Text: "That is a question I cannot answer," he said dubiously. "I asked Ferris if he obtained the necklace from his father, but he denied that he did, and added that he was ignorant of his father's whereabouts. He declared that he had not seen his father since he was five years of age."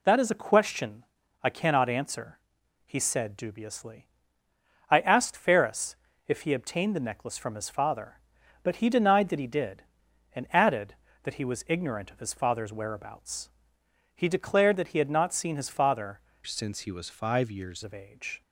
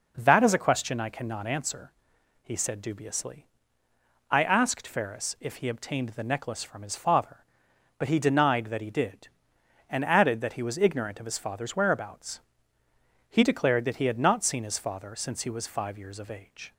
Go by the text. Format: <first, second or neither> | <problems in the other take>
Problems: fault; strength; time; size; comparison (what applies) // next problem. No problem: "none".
second | pauses between "question" and "I"; at 1.0 s; 0.40 s long // pauses between "Ferris" and "if"; slight; at 5.9 s; 0.32 s long // changes voice from "since" to "years"; from 16.4 to 17.8 s; 1.4 s long